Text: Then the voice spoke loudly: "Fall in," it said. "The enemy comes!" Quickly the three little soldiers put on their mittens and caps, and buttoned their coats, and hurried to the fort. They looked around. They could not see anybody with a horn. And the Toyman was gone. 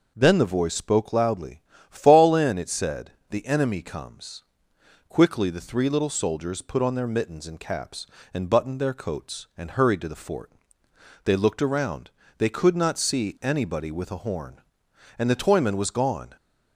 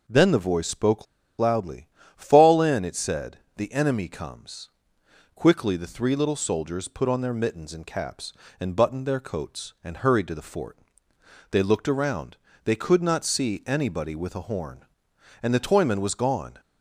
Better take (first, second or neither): first